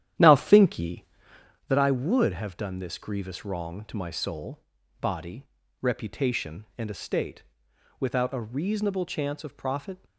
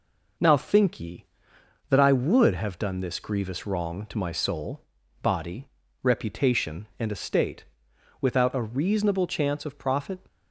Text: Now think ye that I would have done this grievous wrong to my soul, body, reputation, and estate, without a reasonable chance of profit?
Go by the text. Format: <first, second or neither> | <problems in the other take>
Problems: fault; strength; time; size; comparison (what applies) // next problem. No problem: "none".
second | starts louder than the rest; strong; until 1.7 s; 11.5 dB